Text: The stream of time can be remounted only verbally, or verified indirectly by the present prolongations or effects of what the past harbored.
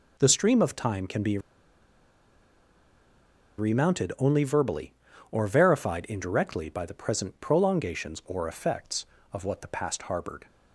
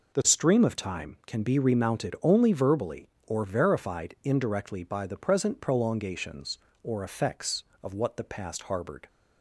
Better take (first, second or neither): second